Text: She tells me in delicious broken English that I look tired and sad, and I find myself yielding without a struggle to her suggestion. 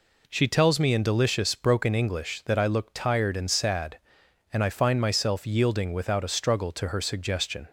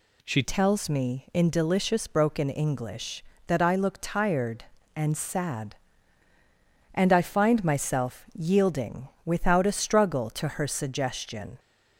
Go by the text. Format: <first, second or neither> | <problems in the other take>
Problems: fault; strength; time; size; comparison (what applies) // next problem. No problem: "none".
first | changes voice at "tells"; from 0.4 s on; 11.1 s long // pauses between "yielding" and "without"; slight; at 9.0 s; 0.16 s long